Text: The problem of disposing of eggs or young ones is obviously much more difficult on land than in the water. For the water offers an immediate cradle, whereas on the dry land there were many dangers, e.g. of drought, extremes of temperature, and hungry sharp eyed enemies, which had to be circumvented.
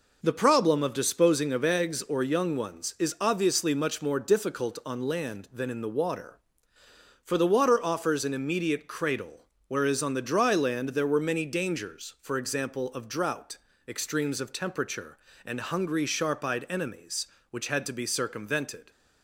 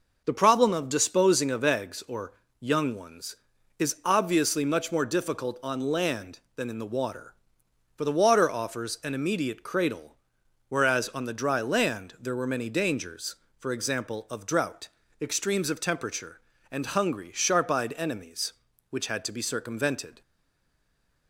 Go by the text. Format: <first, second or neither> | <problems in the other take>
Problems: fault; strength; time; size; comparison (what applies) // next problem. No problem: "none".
first | pauses between "or" and "young"; slight; at 2.3 s; 0.30 s long // stays silent after the last word; from 20.2 s on; 1.0 s long